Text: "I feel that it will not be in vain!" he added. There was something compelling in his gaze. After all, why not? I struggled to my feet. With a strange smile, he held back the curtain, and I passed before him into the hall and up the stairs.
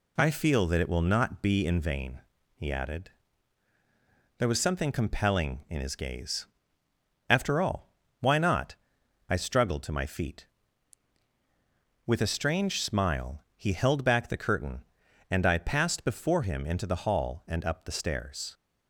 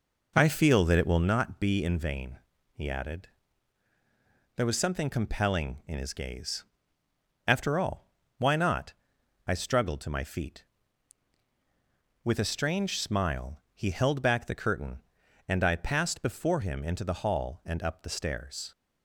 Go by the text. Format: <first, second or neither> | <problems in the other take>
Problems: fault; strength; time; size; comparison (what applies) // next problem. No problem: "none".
first | starts louder than the rest; noticeable; until 1.3 s; 5 dB